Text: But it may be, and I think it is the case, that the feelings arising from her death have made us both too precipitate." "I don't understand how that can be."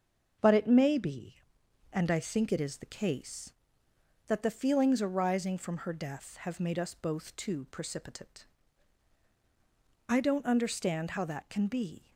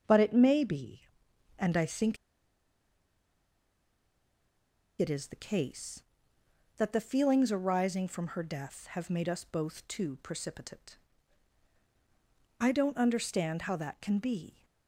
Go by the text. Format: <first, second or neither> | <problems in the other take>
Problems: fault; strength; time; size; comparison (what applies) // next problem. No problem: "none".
first | starts louder than the rest; until 1.6 s; 6.5 dB; also in the first // pauses between "think" and "it"; strong; at 2.1 s; 2.8 s long